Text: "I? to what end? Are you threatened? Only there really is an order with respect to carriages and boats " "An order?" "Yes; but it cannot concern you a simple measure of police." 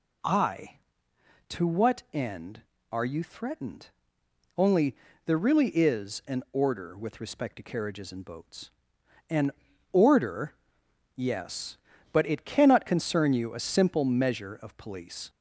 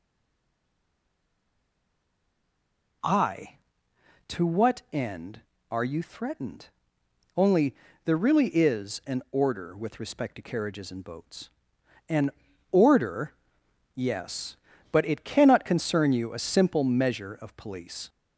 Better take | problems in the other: first | stays silent before the first word; strong; until 3.0 s; 3.0 s long // pauses between "Only" and "there"; slight; at 7.7 s; 0.30 s long; slight in the first // pauses between "An" and "order"; at 12.3 s; 0.40 s long; also in the first

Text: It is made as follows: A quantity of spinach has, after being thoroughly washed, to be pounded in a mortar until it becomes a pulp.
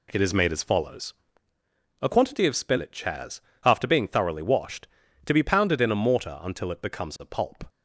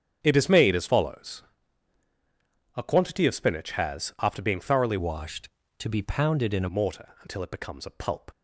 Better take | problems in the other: first | starts louder than the rest; strong; until 1.2 s; 8 dB // changes voice from "washed" to "a"; from 4.9 to 6.6 s; 1.7 s long

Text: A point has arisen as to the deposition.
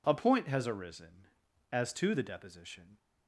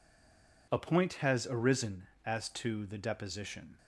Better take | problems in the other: first | stays silent before the first word; slight; until 0.6 s; 0.6 s long

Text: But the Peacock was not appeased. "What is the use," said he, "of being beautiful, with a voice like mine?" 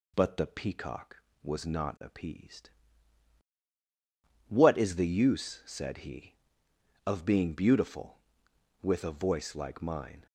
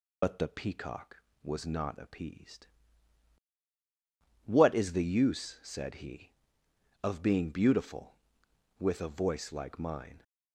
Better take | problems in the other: first | loses the start of "But"; at 0.2 s; 60 ms

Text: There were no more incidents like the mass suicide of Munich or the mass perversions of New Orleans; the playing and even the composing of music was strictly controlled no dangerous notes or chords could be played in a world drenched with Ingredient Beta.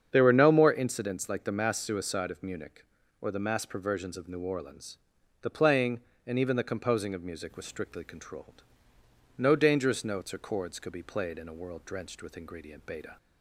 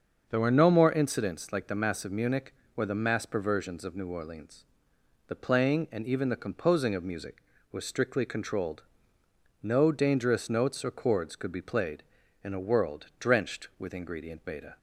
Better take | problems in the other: first | starts louder than the rest; until 1.3 s; 6.5 dB; strong in the first // skips "suicide"; at 2.0 s // pauses between "controlled" and "no"; noticeable; at 8.8 s; 0.80 s long; noticeable in the first

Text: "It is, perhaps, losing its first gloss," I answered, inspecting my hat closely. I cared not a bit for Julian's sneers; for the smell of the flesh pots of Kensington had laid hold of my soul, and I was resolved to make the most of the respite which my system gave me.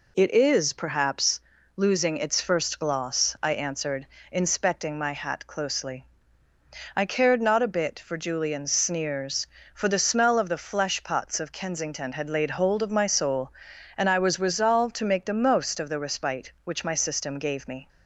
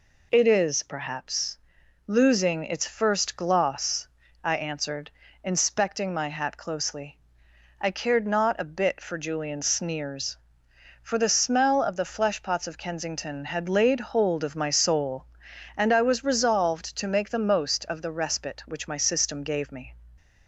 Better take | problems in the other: neither | none

